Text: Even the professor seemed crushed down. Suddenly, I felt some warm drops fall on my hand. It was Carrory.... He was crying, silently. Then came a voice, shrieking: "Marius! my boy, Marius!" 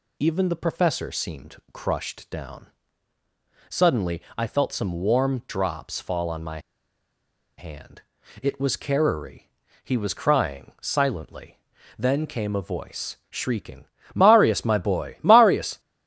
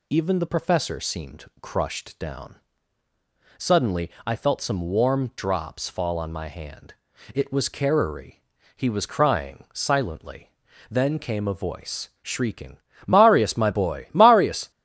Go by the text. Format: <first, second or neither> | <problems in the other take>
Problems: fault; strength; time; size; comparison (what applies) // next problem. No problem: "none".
second | pauses between "my" and "hand"; at 6.5 s; 0.98 s long